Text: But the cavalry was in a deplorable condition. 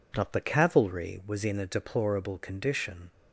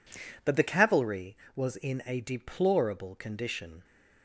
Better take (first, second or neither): second